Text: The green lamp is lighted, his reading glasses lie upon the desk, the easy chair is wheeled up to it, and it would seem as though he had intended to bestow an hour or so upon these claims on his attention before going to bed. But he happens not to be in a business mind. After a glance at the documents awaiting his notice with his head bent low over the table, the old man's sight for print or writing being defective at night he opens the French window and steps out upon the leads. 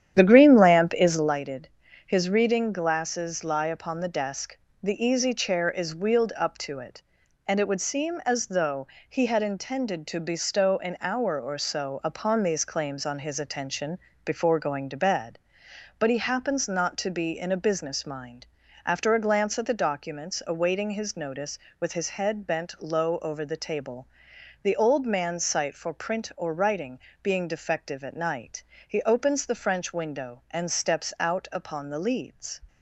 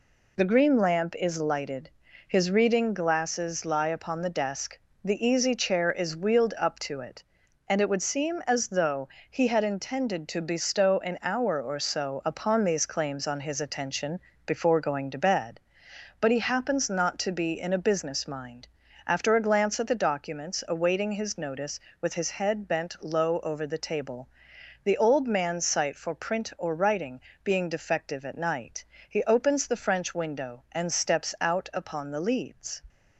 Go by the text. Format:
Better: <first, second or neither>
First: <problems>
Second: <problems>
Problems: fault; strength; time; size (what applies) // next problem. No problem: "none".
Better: second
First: starts louder than the rest; strong; until 1.4 s; 10 dB // pauses between "though" and "he"; slight; at 8.8 s; 0.22 s long // pauses between "attention" and "before"; slight; at 13.9 s; 0.24 s long // pauses between "writing" and "being"; slight; at 26.9 s; 0.24 s long // pauses between "night" and "he"; slight; at 28.6 s; 0.24 s long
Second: pauses between "though" and "he"; slight; at 9.0 s; 0.22 s long // pauses between "attention" and "before"; slight; at 14.2 s; 0.24 s long // pauses between "writing" and "being"; slight; at 27.1 s; 0.24 s long // pauses between "night" and "he"; slight; at 28.8 s; 0.24 s long